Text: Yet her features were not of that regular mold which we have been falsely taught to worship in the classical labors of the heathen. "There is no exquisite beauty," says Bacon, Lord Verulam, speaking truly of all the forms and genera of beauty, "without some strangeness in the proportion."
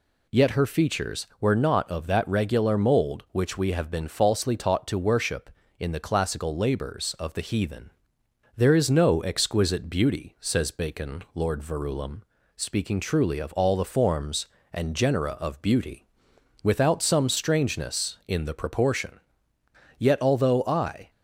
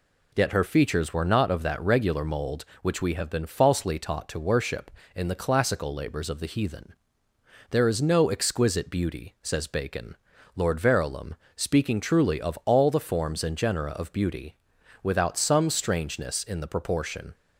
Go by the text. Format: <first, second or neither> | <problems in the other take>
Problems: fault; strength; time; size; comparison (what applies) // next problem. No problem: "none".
second | goes on to say "Yet although I"; noticeable; from 19.9 s on; 1.1 s long